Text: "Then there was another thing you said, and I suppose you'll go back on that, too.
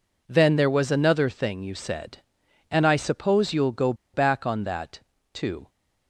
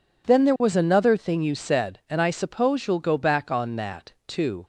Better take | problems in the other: second | pauses between "go" and "back"; slight; at 3.9 s; 0.20 s long

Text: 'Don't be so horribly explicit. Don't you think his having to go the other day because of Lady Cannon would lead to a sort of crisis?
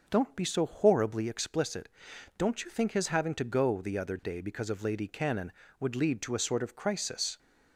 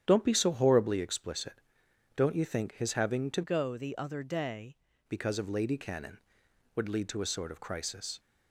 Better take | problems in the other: first | starts louder than the rest; strong; until 1.0 s; 9.5 dB // changes voice from "go" to "day"; from 3.4 to 4.7 s; 1.3 s long

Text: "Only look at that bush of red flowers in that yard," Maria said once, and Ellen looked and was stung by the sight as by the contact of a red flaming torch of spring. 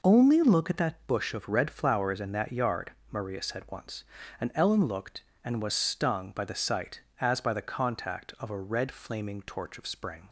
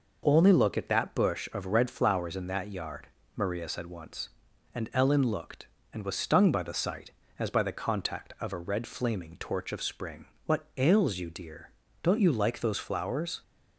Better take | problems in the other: first | goes on to say "What ails you dear don't you like those flowers"; strong; from 10.4 s on; 2.9 s long

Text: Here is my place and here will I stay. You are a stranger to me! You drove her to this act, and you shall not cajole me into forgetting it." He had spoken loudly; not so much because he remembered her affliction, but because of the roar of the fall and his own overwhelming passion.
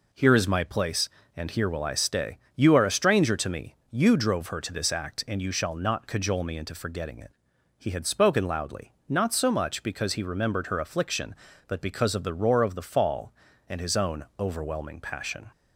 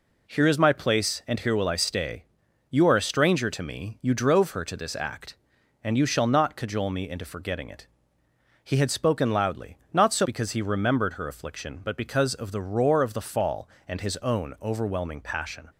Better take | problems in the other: first | skips "much"; at 10.2 s

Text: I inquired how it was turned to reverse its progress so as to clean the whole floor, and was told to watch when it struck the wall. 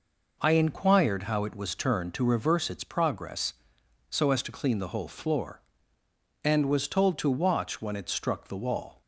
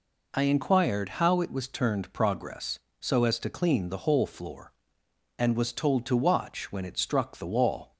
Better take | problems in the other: first | skips "to reverse its"; at 2.1 s

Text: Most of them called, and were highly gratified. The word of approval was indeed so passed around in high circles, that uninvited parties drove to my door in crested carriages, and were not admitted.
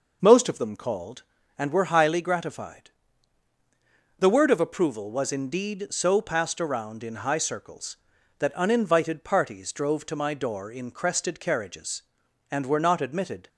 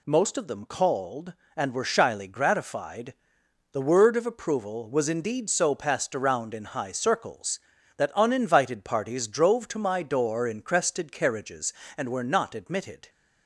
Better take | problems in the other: first | says "shyly" for "highly"; at 1.8 s

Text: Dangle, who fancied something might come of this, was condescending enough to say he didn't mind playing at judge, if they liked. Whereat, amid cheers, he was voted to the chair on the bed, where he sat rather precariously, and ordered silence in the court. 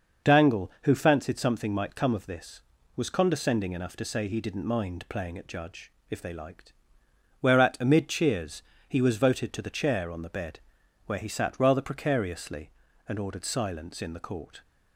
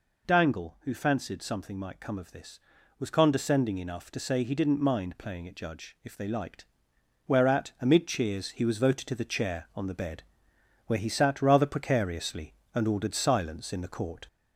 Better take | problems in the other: first | gets louder; slight; throughout; 3 dB

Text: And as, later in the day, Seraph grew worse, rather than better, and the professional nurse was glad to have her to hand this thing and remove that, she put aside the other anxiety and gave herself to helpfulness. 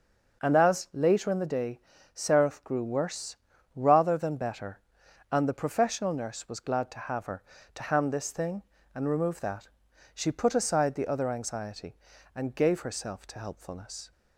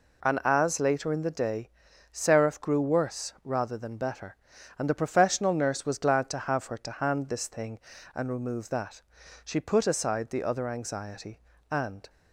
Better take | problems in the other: first | stops before "gave herself to helpfulness"; at 12.0 s

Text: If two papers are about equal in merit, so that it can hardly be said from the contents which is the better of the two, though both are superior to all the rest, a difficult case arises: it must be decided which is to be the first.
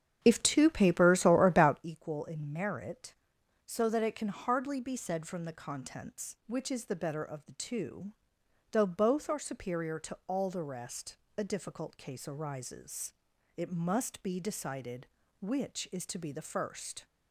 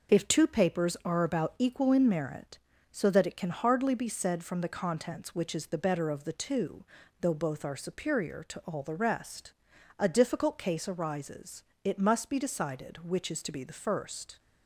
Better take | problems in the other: second | starts louder than the rest; strong; until 1.9 s; 8 dB

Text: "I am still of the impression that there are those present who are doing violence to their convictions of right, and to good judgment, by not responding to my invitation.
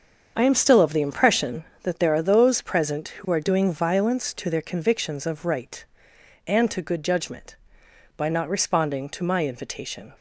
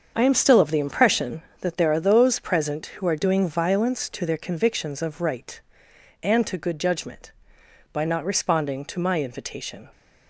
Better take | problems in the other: neither | starts louder than the rest; the same in both

